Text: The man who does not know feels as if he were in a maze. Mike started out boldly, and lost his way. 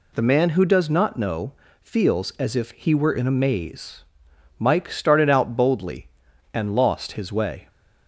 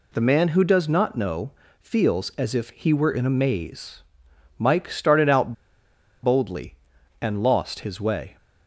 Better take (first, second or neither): first